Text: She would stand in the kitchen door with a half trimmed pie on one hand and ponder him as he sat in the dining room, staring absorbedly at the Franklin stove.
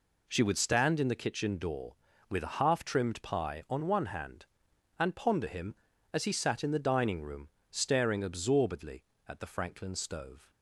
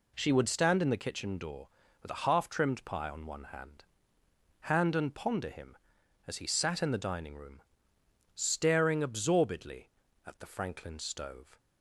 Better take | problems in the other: first | says "hand" twice; at 4.6 s

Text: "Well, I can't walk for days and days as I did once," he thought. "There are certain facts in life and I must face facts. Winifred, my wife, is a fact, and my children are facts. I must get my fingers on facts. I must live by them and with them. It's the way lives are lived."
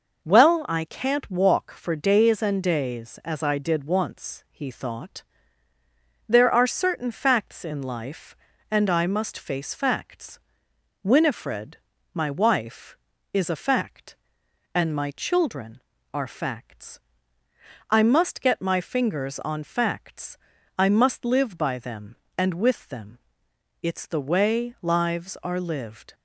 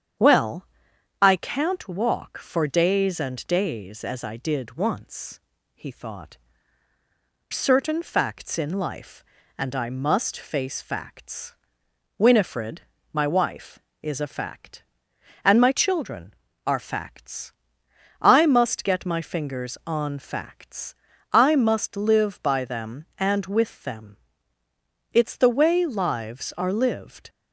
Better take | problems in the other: first | starts louder than the rest; strong; until 1.7 s; 8.5 dB // skips "There are"; at 6.9 s

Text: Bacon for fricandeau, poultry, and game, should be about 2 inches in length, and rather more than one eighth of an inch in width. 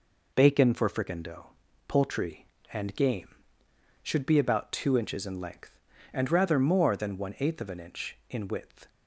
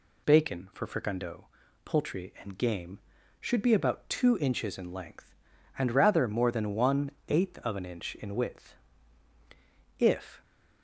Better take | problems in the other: first | pauses between "one" and "eighth"; slight; at 7.0 s; 0.18 s long // goes on to say "If"; slight; from 9.9 s on; 0.44 s long

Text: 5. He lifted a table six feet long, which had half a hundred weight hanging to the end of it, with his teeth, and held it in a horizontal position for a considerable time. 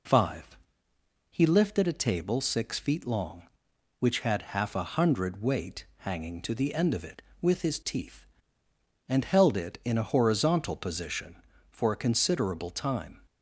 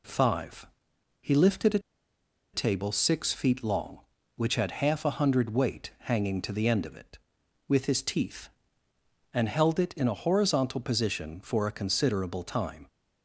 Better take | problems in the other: first | pauses between "a" and "table"; noticeable; at 1.7 s; 0.74 s long

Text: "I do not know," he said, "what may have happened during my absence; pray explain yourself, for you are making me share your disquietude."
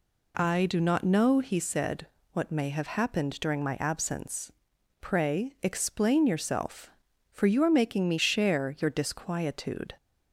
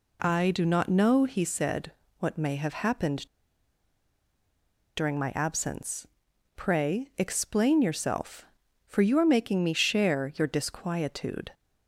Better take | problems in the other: first | pauses between "happened" and "during"; strong; at 3.2 s; 1.7 s long

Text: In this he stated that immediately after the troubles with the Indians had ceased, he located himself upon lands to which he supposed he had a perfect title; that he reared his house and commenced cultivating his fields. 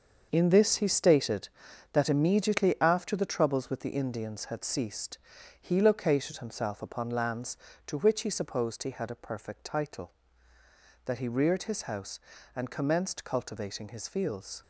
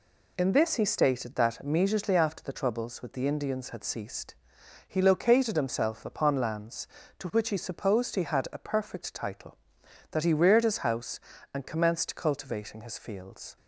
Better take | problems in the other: second | gets quieter; strong; throughout; 9 dB

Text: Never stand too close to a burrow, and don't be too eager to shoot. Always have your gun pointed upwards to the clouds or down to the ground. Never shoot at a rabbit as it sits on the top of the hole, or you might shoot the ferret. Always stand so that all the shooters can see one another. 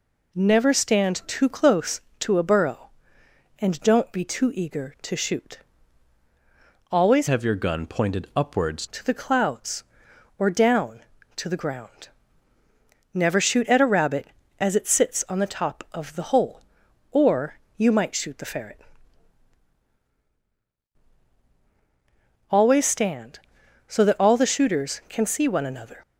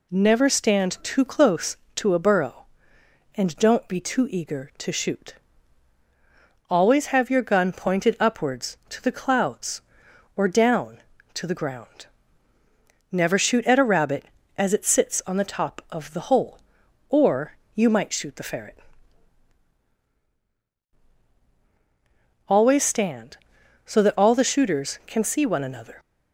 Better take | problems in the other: second | changes voice from "have" to "upwards"; from 7.2 to 8.8 s; 1.6 s long // pauses between "or" and "you"; slight; at 17.5 s; 0.22 s long; slight in the second

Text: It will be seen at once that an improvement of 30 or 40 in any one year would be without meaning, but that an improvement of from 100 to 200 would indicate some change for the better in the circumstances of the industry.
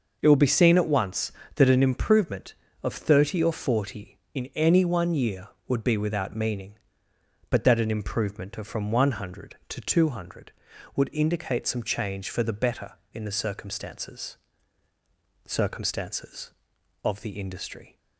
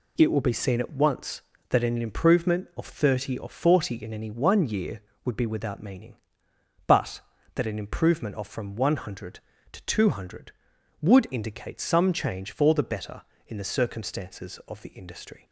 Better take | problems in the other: second | says "circumstances" twice; at 15.4 s

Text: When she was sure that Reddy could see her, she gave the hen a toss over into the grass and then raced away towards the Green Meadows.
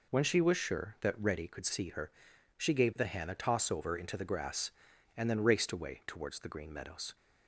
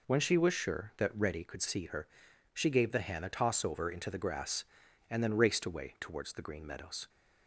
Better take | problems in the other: neither | none

